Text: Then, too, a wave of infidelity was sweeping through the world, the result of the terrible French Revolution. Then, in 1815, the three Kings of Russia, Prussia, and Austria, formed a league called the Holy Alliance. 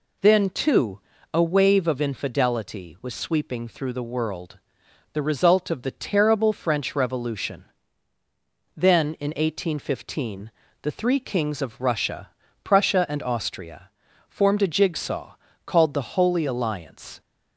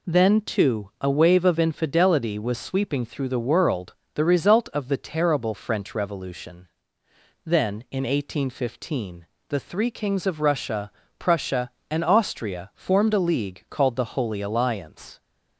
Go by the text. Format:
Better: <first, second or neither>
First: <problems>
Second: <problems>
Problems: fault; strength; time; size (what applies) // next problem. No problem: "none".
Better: second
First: says "jigsaw" for "league"; at 14.6 s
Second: none